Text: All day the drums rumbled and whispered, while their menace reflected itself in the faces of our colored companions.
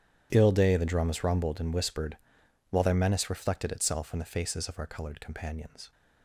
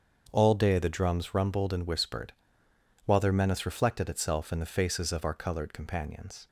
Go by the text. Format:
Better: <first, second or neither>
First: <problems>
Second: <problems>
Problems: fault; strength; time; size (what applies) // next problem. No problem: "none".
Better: second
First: starts louder than the rest; strong; until 1.3 s; 9.5 dB // says "Ill" for "All"; at 0.3 s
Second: starts louder than the rest; until 1.3 s; 7 dB